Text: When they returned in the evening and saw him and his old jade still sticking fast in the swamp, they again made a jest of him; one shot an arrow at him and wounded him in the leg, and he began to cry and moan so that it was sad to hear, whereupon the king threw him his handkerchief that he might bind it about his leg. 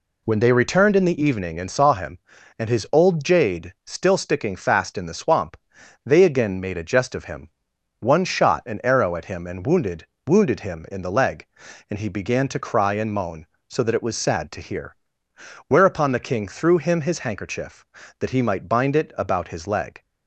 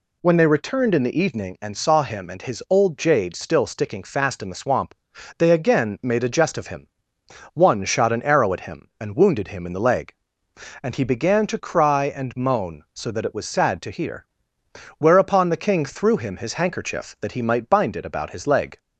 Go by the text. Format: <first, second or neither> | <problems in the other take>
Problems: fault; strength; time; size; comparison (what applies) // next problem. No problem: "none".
second | says "wounded" twice; at 10.2 s